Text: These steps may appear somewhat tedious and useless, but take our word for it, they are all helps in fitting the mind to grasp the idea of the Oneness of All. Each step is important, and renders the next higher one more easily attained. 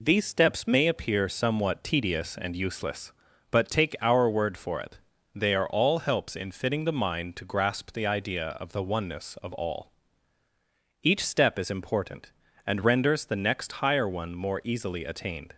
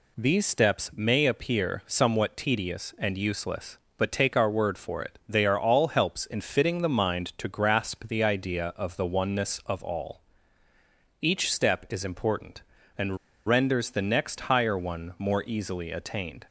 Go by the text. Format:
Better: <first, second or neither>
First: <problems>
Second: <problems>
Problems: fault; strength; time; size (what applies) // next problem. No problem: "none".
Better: first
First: none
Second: pauses between "and" and "renders"; slight; at 13.1 s; 0.29 s long